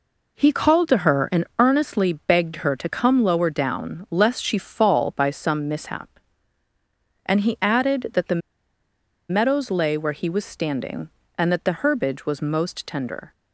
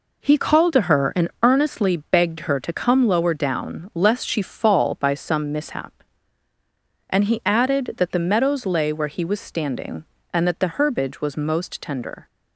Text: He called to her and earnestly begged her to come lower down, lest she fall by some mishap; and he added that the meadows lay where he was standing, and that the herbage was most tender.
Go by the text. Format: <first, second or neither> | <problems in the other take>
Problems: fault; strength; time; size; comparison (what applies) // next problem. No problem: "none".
second | pauses between "the" and "meadows"; noticeable; at 8.4 s; 0.91 s long